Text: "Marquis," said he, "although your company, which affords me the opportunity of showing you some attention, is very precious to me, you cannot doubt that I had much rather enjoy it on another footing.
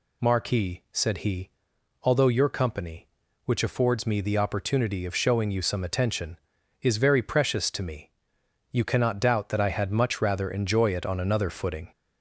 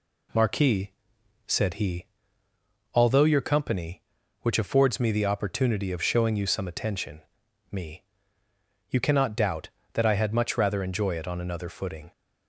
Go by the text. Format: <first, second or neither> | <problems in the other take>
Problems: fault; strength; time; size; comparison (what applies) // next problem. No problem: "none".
first | skips "is very precious to"; at 7.4 s